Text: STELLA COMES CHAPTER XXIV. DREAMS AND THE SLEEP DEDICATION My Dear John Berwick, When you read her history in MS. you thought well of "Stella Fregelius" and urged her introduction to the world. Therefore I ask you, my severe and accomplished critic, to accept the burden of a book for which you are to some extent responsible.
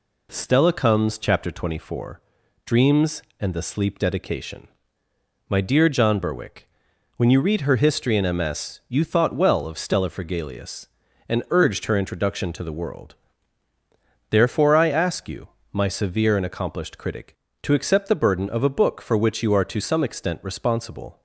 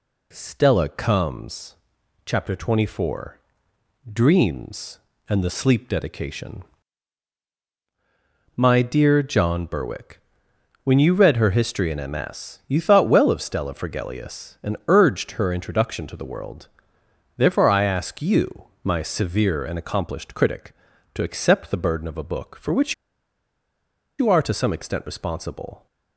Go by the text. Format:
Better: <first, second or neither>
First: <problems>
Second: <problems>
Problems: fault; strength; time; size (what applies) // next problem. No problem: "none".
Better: first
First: pauses between "DEDICATION" and "My"; noticeable; at 4.6 s; 0.80 s long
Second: pauses between "COMES" and "CHAPTER"; noticeable; at 1.7 s; 0.48 s long // pauses between "DEDICATION" and "My"; strong; at 6.6 s; 1.9 s long // pauses between "which" and "you"; strong; at 22.9 s; 1.2 s long